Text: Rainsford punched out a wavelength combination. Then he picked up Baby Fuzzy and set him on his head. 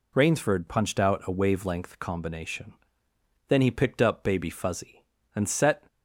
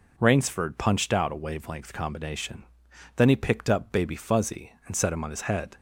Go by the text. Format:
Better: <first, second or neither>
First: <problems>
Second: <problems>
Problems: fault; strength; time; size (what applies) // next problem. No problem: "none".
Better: second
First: stops before "him on his head"; at 5.8 s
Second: none